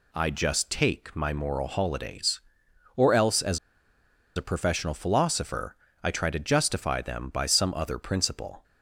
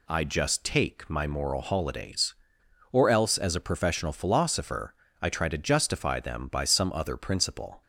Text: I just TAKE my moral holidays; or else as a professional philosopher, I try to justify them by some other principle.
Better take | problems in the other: second | pauses between "as" and "a"; noticeable; at 3.5 s; 0.78 s long

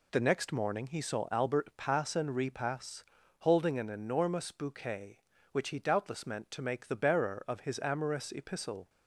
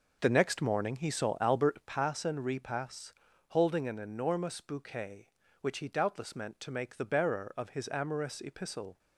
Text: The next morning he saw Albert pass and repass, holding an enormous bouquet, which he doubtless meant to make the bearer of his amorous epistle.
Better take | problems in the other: first | starts louder than the rest; noticeable; until 2.0 s; 5.5 dB

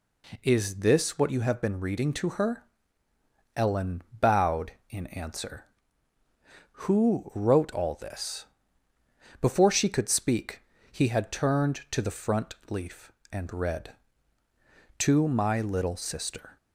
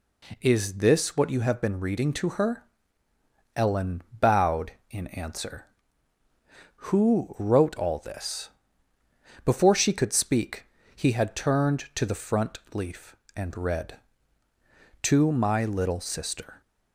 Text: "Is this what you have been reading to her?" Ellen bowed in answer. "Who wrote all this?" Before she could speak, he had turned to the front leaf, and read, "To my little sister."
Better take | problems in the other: neither | pauses between "Ellen" and "bowed"; slight; the same in both // pauses between "front" and "leaf"; slight; the same in both

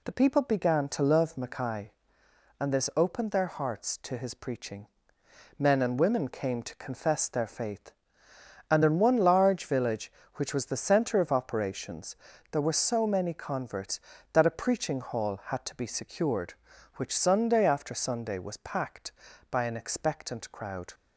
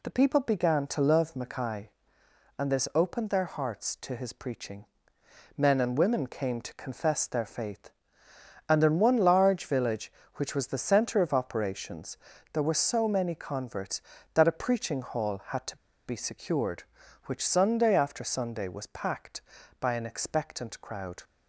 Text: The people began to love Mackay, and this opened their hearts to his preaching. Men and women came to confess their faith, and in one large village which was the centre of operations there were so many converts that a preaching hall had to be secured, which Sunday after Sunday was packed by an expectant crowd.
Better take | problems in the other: first | pauses between "operations" and "there"; at 12.1 s; 0.38 s long; also in the first // pauses between "to" and "be"; slight; at 15.7 s; 0.30 s long

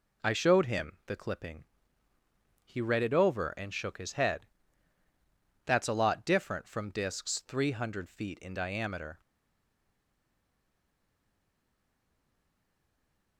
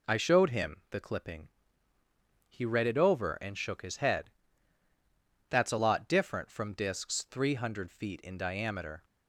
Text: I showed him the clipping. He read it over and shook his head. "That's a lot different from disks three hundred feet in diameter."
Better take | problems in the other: second | stays silent after the last word; strong; from 9.1 s on; 4.2 s long

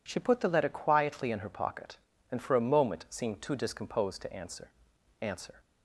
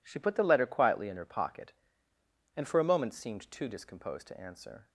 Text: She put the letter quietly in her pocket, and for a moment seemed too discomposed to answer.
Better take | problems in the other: second | says "answer" twice; at 5.2 s

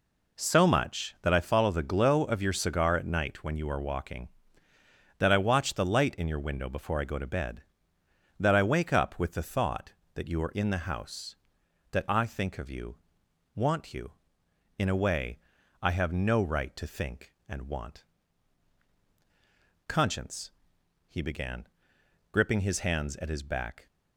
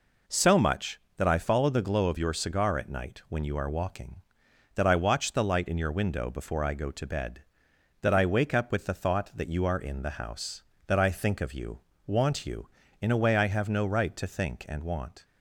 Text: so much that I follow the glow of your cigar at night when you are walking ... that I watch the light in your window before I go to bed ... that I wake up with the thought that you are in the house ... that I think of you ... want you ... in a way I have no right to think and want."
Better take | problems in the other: second | pauses between "way" and "I"; at 15.3 s; 0.42 s long // goes on to say "Conscience he began gripping his hands at his back"; strong; from 19.8 s on; 4.0 s long

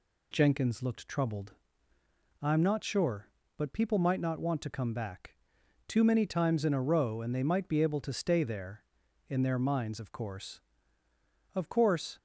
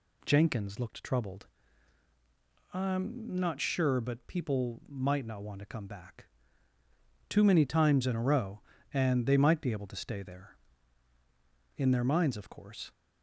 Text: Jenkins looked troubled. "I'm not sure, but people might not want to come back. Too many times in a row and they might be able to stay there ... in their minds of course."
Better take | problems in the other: second | goes on to say "Of course"; noticeable; from 11.5 s on; 0.64 s long

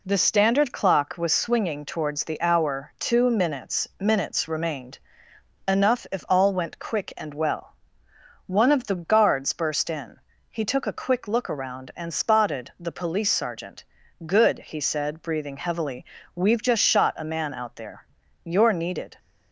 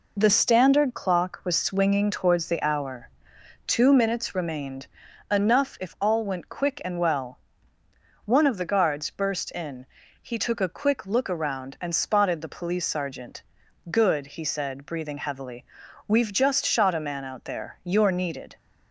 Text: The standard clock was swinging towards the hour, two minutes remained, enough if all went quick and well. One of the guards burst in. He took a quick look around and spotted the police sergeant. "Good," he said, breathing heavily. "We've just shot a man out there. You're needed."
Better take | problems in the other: second | says "minutes" twice; at 3.9 s

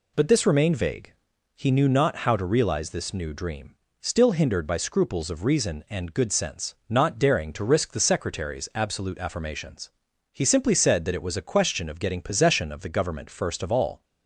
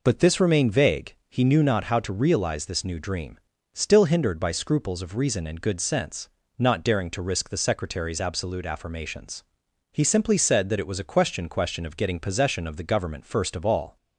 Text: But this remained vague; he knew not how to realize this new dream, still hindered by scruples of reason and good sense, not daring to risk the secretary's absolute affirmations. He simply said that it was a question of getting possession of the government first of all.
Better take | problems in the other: first | says "question" twice; at 11.4 s

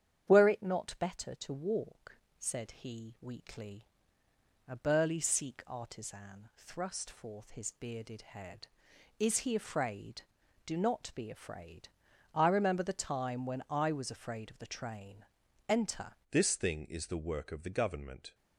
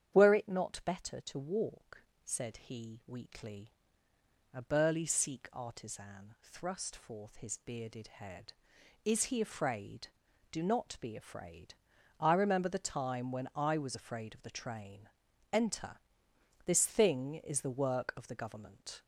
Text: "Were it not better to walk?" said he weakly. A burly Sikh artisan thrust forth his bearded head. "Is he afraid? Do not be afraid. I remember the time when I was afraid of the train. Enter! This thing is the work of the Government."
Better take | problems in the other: second | starts louder than the rest; strong; until 1.2 s; 9 dB; strong in the second // changes voice at "This"; from 16.3 s on; 2.0 s long

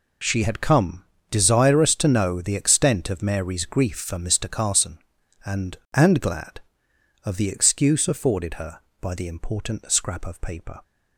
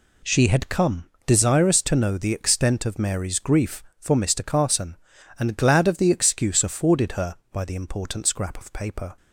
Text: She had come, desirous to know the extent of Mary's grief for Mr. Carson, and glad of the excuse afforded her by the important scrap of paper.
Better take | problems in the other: second | says "and" twice; at 5.9 s

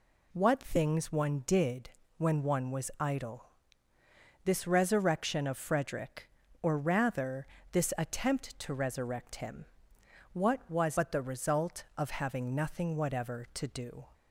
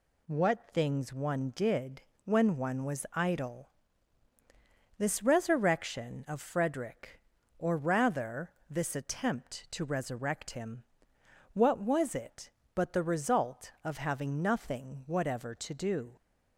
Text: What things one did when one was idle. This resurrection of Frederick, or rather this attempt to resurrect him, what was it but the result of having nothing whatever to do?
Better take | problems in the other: second | pauses between "did" and "when"; slight; at 1.8 s; 0.28 s long; slight in the second // pauses between "rather" and "this"; slight; at 7.4 s; 0.24 s long; slight in the second // skips "it"; at 10.9 s

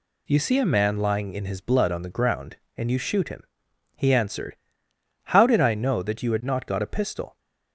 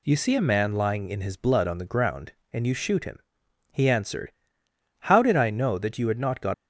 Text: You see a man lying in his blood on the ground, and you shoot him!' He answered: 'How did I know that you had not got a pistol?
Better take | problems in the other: first | stops before "a pistol"; at 6.5 s

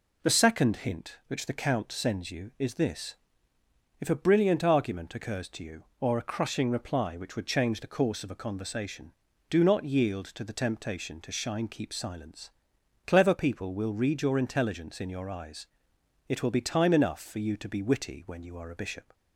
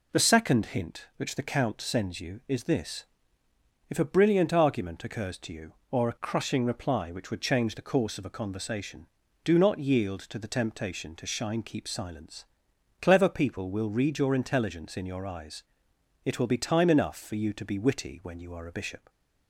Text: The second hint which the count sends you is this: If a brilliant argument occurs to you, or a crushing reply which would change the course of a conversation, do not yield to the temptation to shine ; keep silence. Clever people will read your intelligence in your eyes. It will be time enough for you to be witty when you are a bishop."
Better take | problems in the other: neither | none

